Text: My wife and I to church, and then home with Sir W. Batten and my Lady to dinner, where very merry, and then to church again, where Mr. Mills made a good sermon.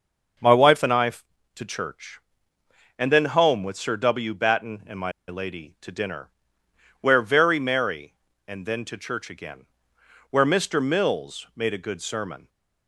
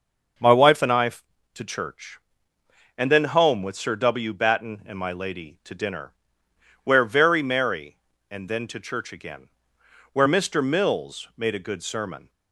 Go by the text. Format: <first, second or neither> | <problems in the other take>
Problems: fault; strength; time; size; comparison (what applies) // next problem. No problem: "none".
second | starts louder than the rest; until 1.8 s; 6.5 dB; also in the second // pauses between "my" and "Lady"; slight; at 5.1 s; 0.16 s long